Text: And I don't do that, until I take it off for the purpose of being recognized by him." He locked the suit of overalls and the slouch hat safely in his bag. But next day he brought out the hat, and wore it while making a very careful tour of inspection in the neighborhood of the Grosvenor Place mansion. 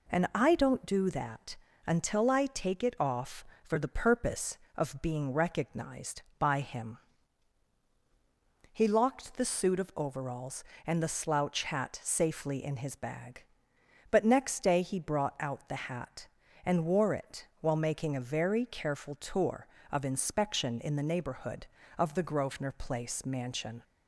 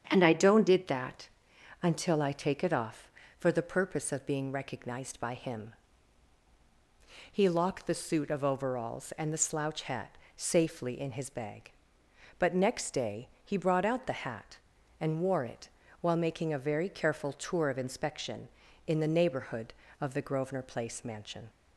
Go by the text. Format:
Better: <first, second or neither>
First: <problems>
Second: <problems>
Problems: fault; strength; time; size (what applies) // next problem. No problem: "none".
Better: first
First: none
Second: starts louder than the rest; strong; until 1.0 s; 8 dB // says "did" for "do"; at 0.6 s // pauses between "hat" and "safely"; slight; at 10.1 s; 0.20 s long // pauses between "it" and "while"; slight; at 15.6 s; 0.34 s long